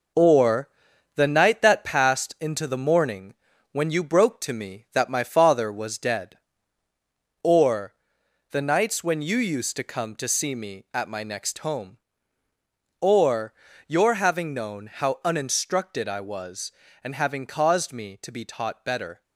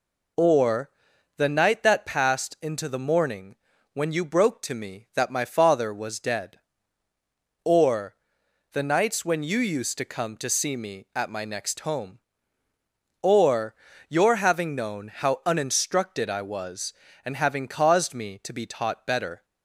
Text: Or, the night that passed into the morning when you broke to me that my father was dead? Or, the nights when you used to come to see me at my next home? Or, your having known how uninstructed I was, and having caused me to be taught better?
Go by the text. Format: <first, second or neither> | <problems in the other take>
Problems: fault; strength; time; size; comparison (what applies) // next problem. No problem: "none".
second | gets quieter; strong; throughout; 7 dB // pauses between "morning" and "when"; at 3.3 s; 0.38 s long; also in the second